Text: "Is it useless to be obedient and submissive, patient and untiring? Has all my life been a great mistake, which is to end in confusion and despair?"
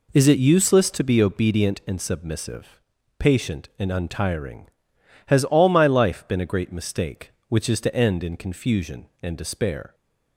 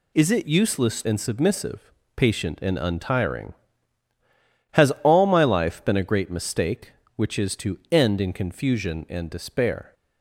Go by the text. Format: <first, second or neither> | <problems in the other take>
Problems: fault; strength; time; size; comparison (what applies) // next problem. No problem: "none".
first | skips "to be obedient"; at 1.0 s